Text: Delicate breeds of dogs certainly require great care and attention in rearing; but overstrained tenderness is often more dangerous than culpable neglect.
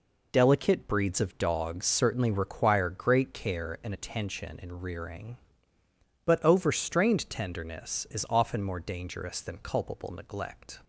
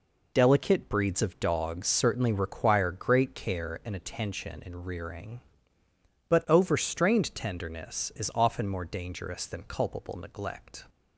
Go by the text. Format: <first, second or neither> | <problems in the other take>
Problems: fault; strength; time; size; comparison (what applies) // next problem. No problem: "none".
neither | none